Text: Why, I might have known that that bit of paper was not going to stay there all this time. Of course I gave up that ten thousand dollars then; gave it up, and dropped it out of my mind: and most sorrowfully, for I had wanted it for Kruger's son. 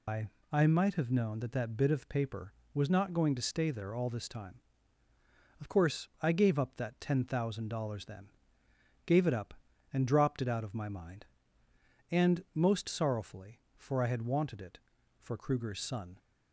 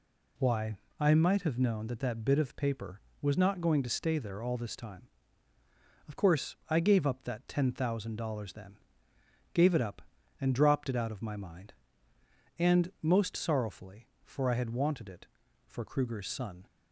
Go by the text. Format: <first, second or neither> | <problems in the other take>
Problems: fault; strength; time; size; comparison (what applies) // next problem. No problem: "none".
second | loses the start of "Why"; at 0.0 s; 175 ms